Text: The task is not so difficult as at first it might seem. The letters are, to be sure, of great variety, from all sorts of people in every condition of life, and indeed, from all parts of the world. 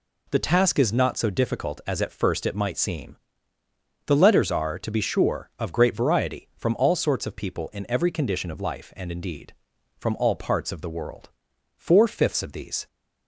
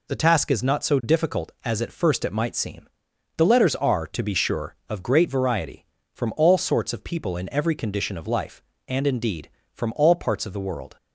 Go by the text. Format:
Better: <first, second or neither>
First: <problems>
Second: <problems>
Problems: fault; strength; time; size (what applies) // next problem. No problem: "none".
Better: second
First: goes on to say "Four fifths of these"; noticeable; from 11.7 s on; 1.1 s long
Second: none